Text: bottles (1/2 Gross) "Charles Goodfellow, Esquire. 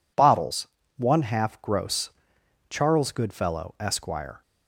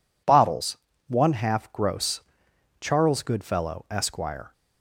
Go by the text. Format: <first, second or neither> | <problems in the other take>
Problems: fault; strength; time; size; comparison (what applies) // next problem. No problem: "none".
neither | none